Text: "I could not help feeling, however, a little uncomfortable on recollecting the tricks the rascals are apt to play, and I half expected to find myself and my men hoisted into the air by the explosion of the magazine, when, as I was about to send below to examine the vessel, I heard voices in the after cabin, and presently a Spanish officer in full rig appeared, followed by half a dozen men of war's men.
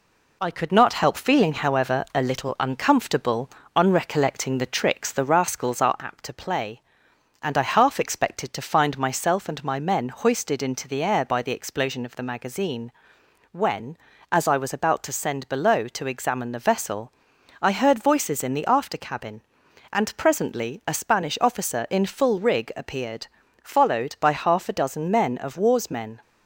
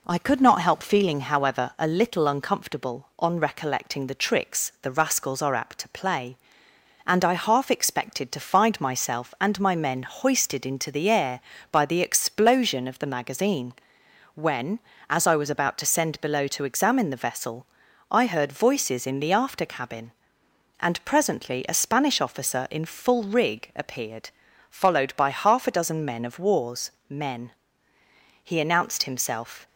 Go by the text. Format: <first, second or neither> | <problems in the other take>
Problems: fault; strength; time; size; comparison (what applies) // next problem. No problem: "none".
first | pauses between "war's" and "men"; slight; at 26.8 s; 0.18 s long // goes on to say "He announced himself"; noticeable; from 28.4 s on; 1.2 s long